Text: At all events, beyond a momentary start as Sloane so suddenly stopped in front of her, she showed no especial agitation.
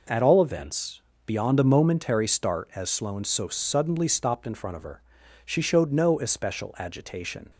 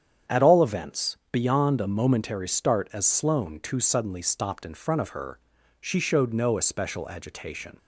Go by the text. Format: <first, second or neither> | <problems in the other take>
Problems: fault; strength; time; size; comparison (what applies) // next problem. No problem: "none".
first | starts louder than the rest; strong; until 1.4 s; 8.5 dB // says "too" for "so"; at 3.6 s